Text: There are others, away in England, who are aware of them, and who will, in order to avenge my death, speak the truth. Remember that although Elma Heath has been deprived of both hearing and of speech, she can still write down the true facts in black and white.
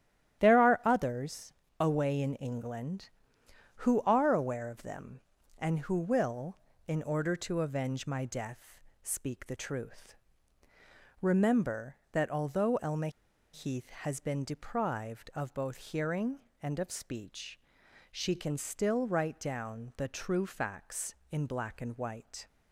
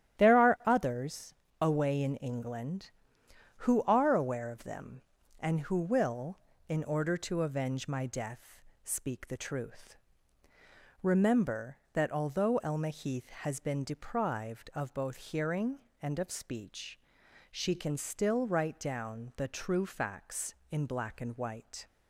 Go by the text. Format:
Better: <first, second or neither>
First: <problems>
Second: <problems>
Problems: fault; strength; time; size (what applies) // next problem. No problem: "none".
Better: second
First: starts louder than the rest; strong; until 1.4 s; 11.5 dB // pauses between "Elma" and "Heath"; at 13.0 s; 0.44 s long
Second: starts louder than the rest; strong; until 1.2 s; 11.5 dB